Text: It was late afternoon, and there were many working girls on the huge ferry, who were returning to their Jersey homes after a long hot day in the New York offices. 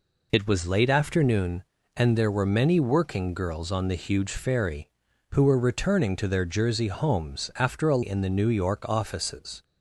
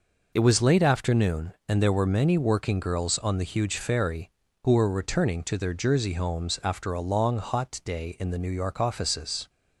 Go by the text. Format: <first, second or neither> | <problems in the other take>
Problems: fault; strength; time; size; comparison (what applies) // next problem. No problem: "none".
second | skips "long hot day"; at 8.0 s